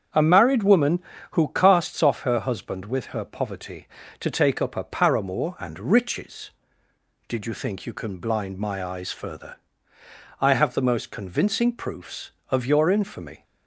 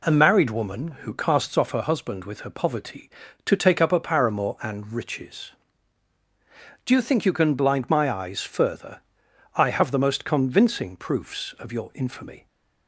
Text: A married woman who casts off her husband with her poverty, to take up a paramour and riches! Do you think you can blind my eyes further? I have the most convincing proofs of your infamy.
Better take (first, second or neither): second